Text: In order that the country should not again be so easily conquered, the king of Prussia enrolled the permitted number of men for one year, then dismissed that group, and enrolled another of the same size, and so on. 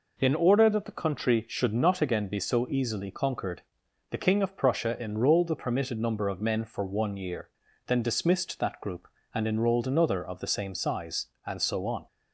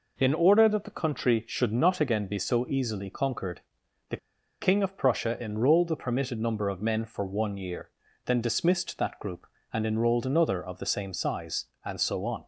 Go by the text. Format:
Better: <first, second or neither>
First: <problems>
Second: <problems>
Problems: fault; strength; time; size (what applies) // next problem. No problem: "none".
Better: first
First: none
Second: pauses between "the" and "king"; at 4.1 s; 0.44 s long